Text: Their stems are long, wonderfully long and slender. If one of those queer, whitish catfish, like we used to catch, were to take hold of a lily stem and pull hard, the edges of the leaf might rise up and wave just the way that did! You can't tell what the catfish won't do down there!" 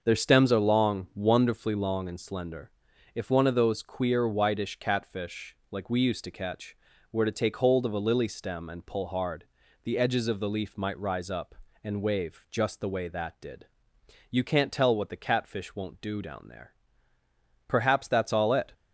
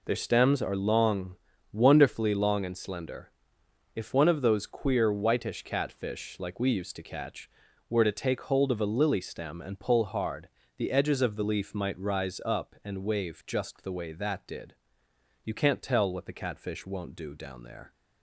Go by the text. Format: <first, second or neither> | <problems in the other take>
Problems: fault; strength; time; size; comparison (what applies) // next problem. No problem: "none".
second | starts louder than the rest; until 1.0 s; 6.5 dB // goes on to say "Perhaps that's all it"; noticeable; from 17.8 s on; 0.92 s long